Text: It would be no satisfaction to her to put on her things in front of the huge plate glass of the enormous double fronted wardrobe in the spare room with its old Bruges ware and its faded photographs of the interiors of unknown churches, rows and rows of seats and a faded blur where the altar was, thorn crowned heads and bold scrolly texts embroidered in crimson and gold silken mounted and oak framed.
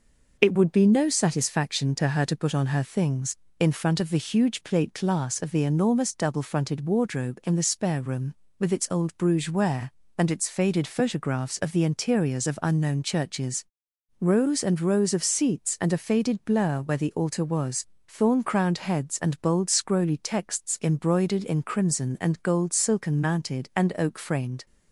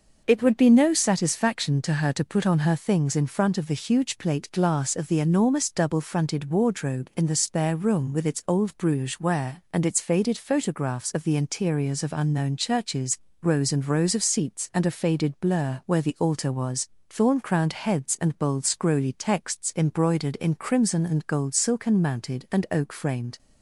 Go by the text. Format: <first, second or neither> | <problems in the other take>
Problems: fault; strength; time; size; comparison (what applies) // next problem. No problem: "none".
neither | none